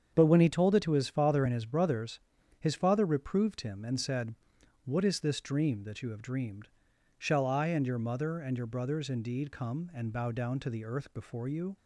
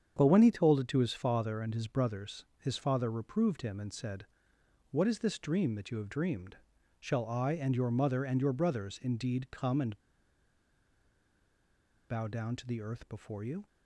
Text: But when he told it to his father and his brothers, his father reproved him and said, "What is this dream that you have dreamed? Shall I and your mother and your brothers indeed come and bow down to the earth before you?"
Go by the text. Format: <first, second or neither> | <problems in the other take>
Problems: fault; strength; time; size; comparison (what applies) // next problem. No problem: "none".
first | starts louder than the rest; strong; until 1.1 s; 8 dB; strong in the first // pauses between "and" and "bow"; strong; at 9.9 s; 2.1 s long